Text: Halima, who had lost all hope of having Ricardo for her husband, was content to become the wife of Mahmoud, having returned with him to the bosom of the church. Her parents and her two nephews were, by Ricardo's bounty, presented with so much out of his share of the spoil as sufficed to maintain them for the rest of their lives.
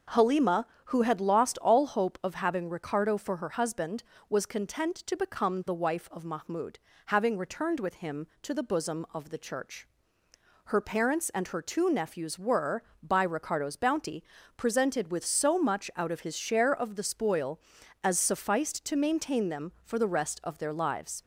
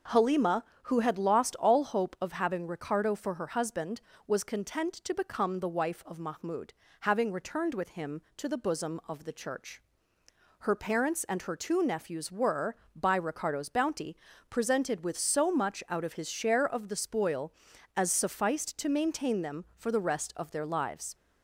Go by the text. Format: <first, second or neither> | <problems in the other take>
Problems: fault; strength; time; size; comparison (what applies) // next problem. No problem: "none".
neither | starts louder than the rest; the same in both